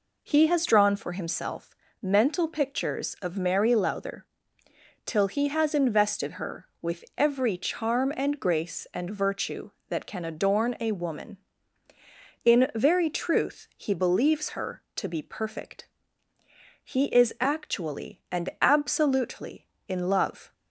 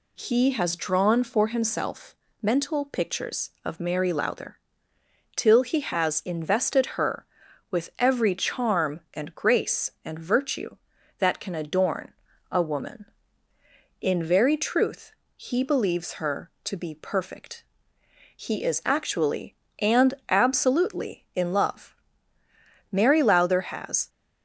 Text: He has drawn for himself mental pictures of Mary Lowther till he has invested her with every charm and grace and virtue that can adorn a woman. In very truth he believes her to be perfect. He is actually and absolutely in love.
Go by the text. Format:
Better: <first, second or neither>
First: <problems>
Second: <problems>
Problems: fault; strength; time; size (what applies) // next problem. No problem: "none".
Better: first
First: pauses between "himself" and "mental"; slight; at 1.7 s; 0.28 s long // pauses between "Lowther" and "till"; noticeable; at 4.2 s; 0.80 s long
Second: pauses between "himself" and "mental"; slight; at 2.1 s; 0.26 s long // pauses between "Lowther" and "till"; noticeable; at 4.5 s; 0.78 s long // pauses between "adorn" and "a"; at 12.1 s; 0.38 s long // pauses between "truth" and "he"; slight; at 15.1 s; 0.22 s long // pauses between "and" and "absolutely"; slight; at 20.1 s; 0.16 s long // goes on to say "Mary Lowther has"; noticeable; from 22.9 s on; 1.1 s long